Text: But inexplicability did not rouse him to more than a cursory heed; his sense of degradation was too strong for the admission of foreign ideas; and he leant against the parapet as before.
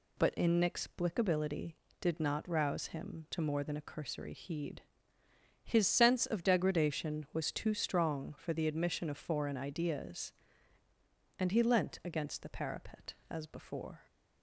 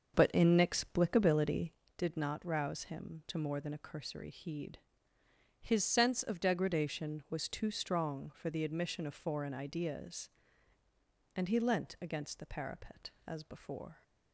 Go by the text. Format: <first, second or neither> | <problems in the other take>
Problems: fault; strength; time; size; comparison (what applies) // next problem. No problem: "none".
first | starts louder than the rest; until 1.8 s; 6 dB